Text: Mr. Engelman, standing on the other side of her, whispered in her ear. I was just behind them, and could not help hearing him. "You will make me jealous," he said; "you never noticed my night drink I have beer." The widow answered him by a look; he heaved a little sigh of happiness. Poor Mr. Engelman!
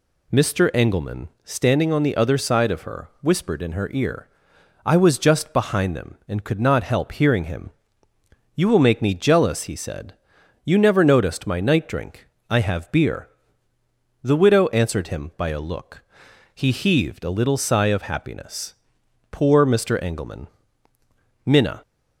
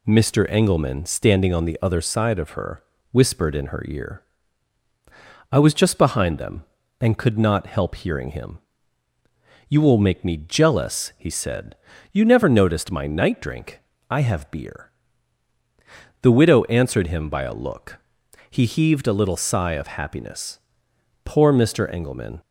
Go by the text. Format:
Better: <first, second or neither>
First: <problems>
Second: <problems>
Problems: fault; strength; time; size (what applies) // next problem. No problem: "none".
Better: second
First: pauses between "drink" and "I"; slight; at 12.2 s; 0.20 s long // goes on to say "Minna"; slight; from 21.4 s on; 0.38 s long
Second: pauses between "drink" and "I"; slight; at 13.7 s; 0.30 s long